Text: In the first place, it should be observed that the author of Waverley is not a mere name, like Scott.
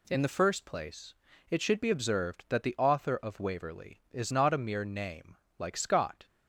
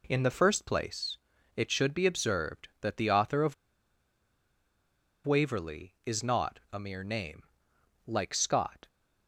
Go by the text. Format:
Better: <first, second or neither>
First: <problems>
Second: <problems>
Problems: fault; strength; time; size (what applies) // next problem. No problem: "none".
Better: first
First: none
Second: pauses between "of" and "Waverley"; strong; at 3.5 s; 1.7 s long